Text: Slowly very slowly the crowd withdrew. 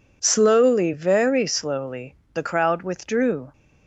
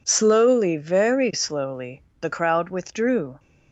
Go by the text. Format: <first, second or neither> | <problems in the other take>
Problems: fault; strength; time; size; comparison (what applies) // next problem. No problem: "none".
neither | pauses between "slowly" and "the"; slight; the same in both